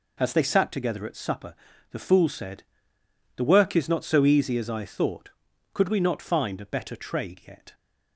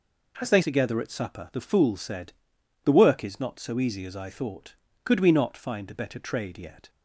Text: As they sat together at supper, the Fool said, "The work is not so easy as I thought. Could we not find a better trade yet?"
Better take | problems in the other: first | skips "sat"; at 0.6 s

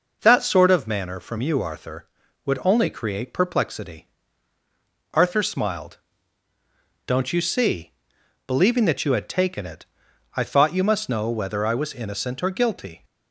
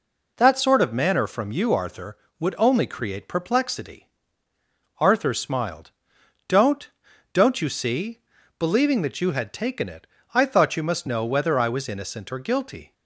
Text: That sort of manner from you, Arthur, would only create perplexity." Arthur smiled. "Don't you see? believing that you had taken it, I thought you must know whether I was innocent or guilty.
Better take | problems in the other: first | says "Don't" twice; at 7.3 s

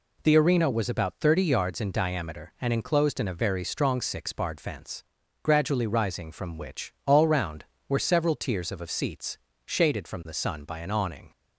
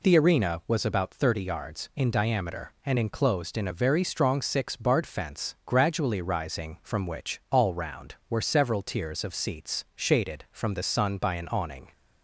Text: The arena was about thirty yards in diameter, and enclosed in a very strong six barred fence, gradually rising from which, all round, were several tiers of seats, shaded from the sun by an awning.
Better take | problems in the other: second | says "of" twice; at 8.8 s

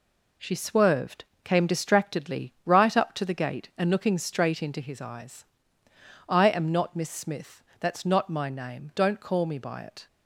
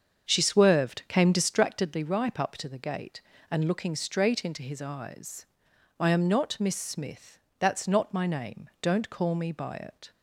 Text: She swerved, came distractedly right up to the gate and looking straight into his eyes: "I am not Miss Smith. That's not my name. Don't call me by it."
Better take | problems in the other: first | starts louder than the rest; until 1.3 s; 7 dB // says "ripe" for "right"; at 2.0 s

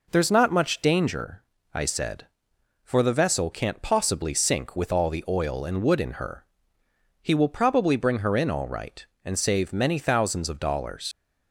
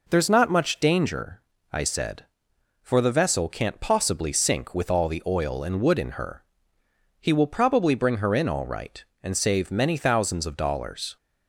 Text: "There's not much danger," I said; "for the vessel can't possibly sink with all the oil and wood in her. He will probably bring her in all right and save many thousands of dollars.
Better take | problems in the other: second | leaves "dollars" unfinished; at 11.1 s; 80 ms

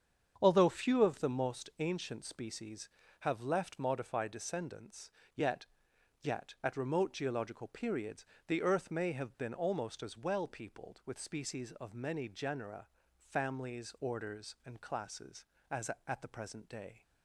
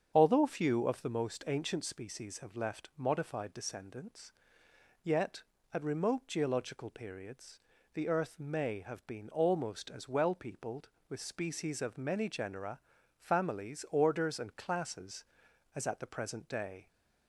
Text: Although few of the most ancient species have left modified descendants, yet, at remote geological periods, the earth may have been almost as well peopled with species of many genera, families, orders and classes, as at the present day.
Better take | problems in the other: second | starts louder than the rest; strong; until 1.4 s; 7.5 dB; strong in the second // says "yet" twice; at 6.2 s

